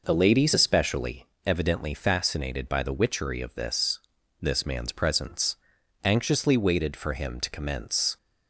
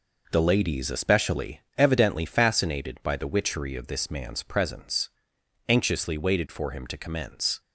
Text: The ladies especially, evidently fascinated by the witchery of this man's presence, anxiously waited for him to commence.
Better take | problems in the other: second | says "this" twice; at 4.4 s

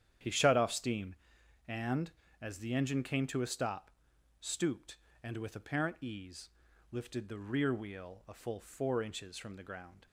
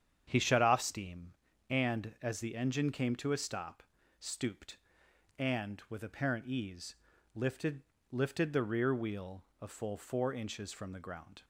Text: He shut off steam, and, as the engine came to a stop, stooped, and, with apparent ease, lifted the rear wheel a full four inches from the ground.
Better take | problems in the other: first | starts louder than the rest; strong; until 1.2 s; 8.5 dB; strong in the first // says "lifted" twice; at 8.1 s // pauses between "wheel" and "a"; slight; at 9.4 s; 0.18 s long

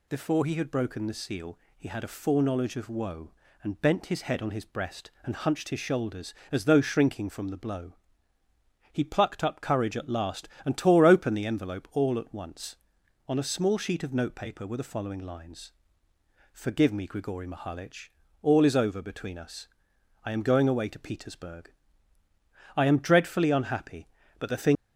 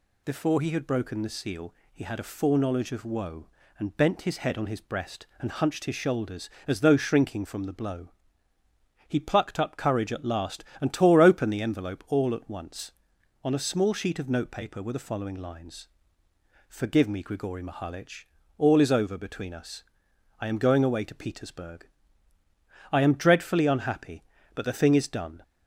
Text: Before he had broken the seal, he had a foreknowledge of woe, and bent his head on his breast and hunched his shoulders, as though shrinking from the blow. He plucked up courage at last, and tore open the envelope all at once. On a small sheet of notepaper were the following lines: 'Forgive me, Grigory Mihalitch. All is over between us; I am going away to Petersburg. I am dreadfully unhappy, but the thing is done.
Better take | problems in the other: second | stops before "is done"; at 24.7 s

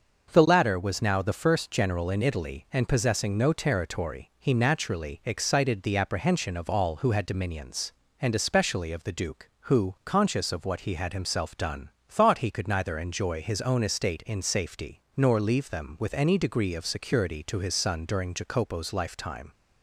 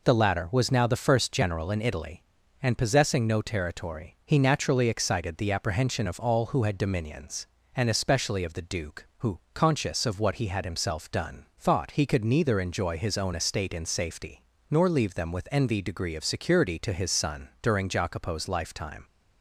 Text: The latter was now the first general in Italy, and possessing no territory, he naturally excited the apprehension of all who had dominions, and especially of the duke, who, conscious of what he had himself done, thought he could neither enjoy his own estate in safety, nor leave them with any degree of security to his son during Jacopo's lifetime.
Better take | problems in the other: first | says "envy" for "any"; at 15.5 s

